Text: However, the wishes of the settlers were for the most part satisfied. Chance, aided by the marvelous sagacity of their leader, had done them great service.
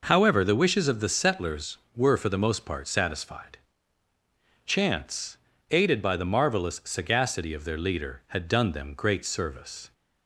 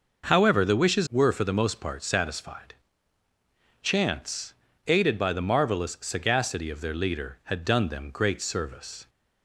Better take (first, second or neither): first